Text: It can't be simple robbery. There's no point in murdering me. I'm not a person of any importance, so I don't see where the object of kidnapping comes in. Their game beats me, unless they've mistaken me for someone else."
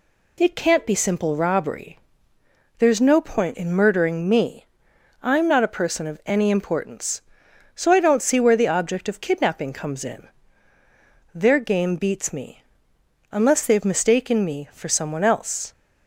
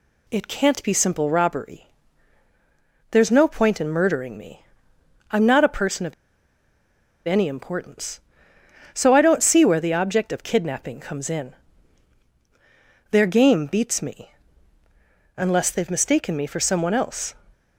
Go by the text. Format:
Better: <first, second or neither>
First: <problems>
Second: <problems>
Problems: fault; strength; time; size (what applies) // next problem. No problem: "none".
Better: first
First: none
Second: pauses between "of" and "any"; at 6.1 s; 1.1 s long